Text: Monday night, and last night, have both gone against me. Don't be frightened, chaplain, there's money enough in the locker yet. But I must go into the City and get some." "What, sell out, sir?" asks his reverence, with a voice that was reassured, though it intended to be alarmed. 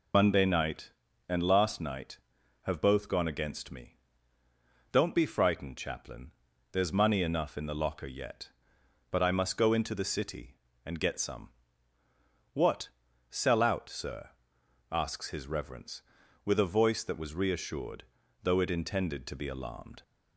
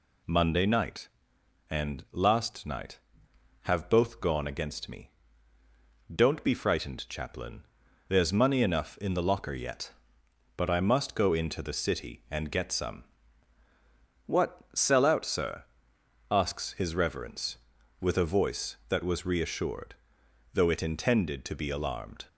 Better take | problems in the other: second | loses the start of "Monday"; at 0.1 s; 45 ms

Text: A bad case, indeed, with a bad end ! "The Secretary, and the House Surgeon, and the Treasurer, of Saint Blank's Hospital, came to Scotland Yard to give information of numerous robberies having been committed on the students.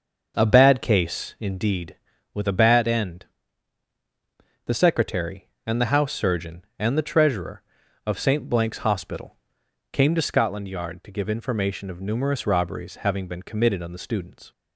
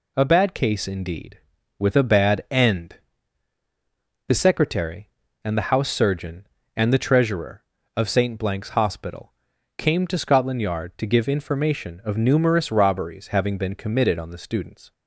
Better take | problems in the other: second | starts louder than the rest; until 1.8 s; 6 dB

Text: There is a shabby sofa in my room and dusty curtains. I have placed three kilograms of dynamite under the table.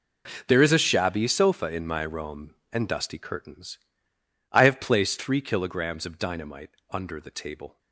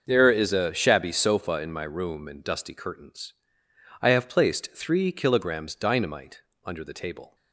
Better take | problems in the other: first | starts louder than the rest; until 1.0 s; 6.5 dB // skips "of"; at 5.7 s // pauses between "dynamite" and "under"; slight; at 6.4 s; 0.24 s long; slight in the first

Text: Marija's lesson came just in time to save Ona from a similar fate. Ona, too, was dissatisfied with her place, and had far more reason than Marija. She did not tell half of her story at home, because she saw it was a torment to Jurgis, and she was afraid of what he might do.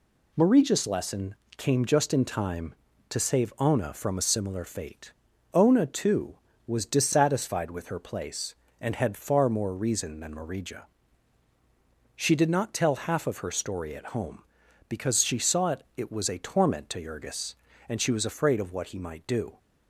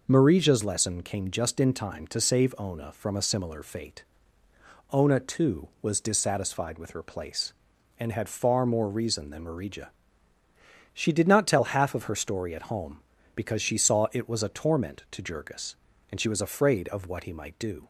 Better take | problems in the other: second | pauses between "lesson" and "came"; slight; at 1.3 s; 0.22 s long // says "it" twice; at 15.9 s

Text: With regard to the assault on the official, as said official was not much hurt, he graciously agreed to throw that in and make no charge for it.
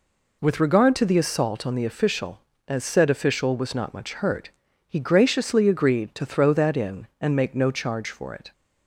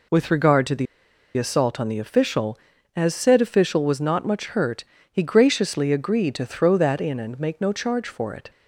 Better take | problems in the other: first | pauses between "the" and "assault"; noticeable; at 0.8 s; 0.52 s long

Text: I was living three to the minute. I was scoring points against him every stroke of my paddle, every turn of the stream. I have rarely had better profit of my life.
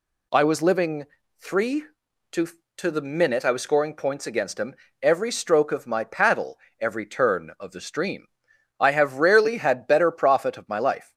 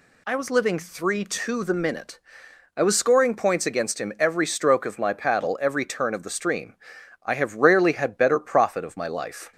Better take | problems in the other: second | pauses between "living" and "three"; slight; at 1.0 s; 0.36 s long // says "to" twice; at 2.7 s // pauses between "him" and "every"; slight; at 4.7 s; 0.26 s long

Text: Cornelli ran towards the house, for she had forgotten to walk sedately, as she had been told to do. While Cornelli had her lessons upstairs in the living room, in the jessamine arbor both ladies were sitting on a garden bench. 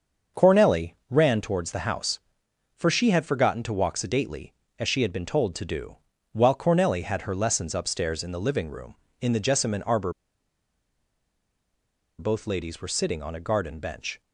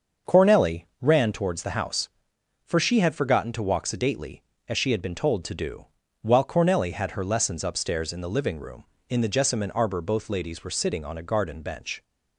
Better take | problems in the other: second | starts louder than the rest; until 1.5 s; 6.5 dB; also in the second // pauses between "Cornelli" and "ran"; slight; at 0.9 s; 0.16 s long; slight in the second // pauses between "arbor" and "both"; strong; at 10.1 s; 2.0 s long

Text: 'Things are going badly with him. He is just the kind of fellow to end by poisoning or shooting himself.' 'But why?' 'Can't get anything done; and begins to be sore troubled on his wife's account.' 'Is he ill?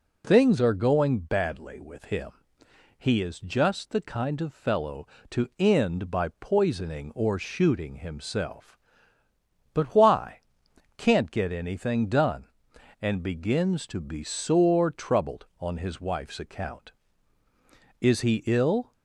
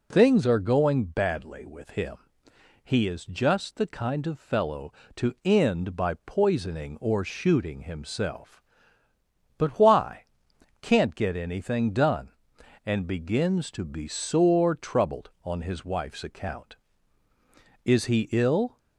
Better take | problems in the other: neither | none

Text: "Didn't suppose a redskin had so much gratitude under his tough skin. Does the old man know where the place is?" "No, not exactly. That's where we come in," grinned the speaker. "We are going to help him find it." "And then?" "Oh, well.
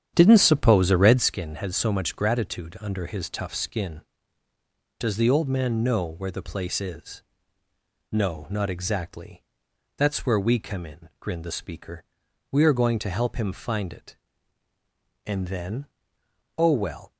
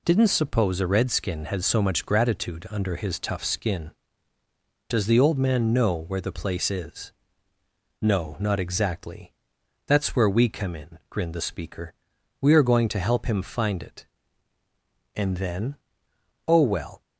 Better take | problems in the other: second | starts louder than the rest; strong; until 1.4 s; 9 dB

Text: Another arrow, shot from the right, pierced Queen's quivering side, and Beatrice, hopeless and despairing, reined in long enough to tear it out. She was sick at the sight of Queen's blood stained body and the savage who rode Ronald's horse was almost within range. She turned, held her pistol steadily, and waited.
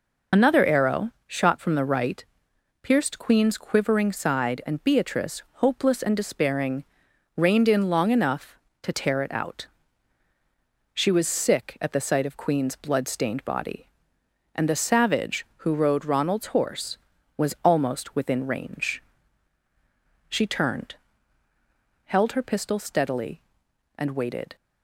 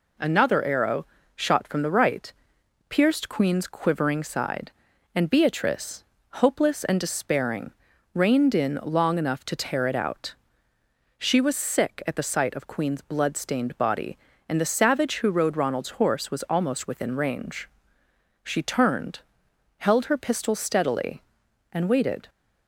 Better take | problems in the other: second | loses the start of "Another"; at 0.3 s; 45 ms

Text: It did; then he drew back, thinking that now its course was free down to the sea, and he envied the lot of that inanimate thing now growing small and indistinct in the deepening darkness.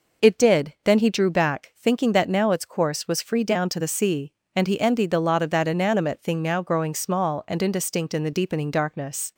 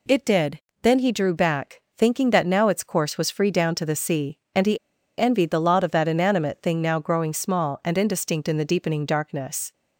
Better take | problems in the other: first | pauses between "he" and "envied"; at 4.7 s; 0.40 s long

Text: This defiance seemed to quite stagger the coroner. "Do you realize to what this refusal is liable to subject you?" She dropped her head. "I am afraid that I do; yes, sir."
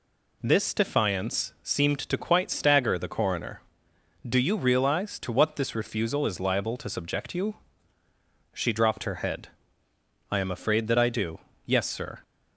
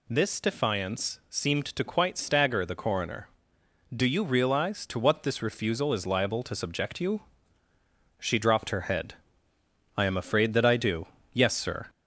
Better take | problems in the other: first | gets louder; slight; throughout; 2.5 dB

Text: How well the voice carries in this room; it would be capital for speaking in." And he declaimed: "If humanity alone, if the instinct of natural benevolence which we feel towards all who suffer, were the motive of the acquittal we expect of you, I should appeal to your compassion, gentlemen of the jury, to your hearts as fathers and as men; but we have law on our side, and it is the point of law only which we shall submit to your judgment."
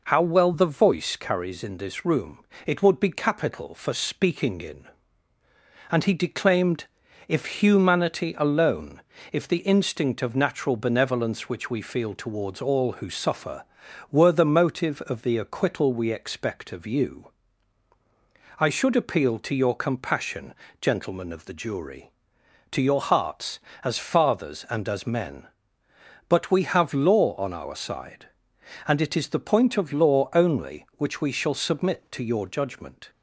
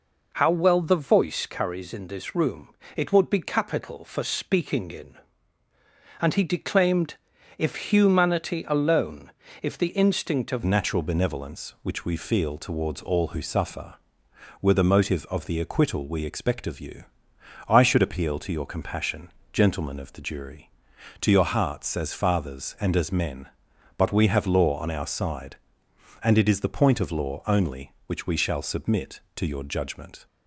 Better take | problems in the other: first | changes voice at "natural"; from 10.6 s on; 19.6 s long

